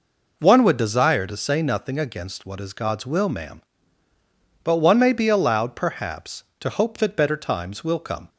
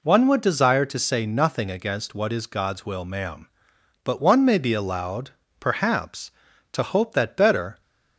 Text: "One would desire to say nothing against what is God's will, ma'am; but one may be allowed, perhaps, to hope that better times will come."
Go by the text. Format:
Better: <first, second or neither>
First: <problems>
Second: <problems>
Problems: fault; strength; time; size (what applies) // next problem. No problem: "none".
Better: first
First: none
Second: stops before "times will come"; at 7.8 s